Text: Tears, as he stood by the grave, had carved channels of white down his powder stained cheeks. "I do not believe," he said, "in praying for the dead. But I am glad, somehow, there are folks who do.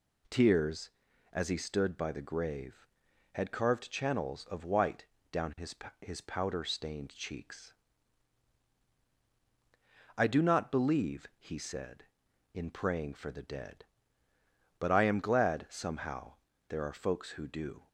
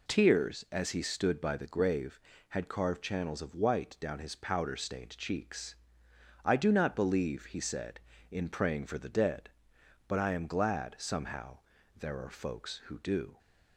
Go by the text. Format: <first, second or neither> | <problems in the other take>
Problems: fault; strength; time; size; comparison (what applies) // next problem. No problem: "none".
second | pauses between "white" and "down"; slight; at 5.0 s; 0.24 s long // says "his" twice; at 6.0 s